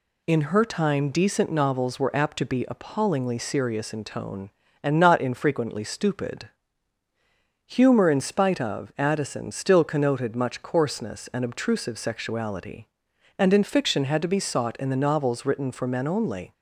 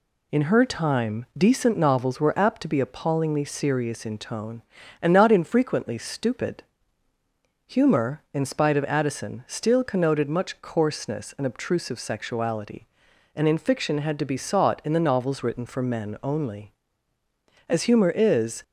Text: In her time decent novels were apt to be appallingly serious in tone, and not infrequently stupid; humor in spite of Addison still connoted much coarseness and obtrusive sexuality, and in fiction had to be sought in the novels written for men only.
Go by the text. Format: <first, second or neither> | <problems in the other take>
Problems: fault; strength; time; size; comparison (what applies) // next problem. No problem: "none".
first | goes on to say "As humor is"; noticeable; from 17.6 s on; 0.94 s long